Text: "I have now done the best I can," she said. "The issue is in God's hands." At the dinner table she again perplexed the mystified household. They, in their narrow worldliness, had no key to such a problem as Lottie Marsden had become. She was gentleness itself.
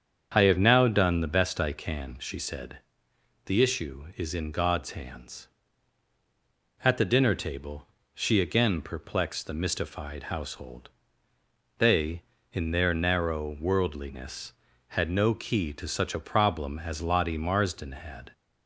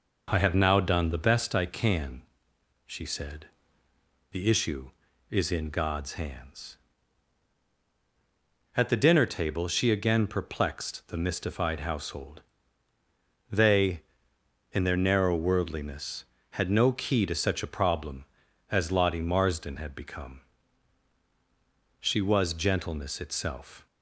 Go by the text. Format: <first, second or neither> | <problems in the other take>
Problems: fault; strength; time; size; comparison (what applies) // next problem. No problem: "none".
second | starts louder than the rest; strong; until 1.3 s; 7.5 dB // pauses between "table" and "she"; slight; at 7.8 s; 0.26 s long // stops before "become She was gentleness itself"; at 18.3 s